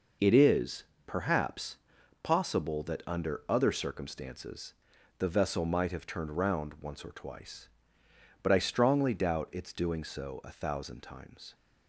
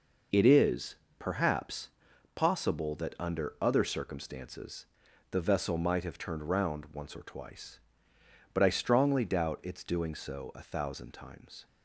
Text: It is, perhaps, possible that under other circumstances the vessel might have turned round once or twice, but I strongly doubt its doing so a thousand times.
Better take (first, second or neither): neither